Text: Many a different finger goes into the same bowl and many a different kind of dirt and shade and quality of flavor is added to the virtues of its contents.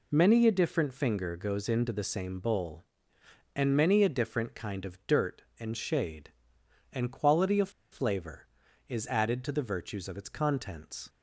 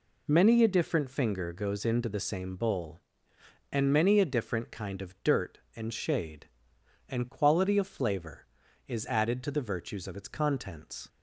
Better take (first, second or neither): second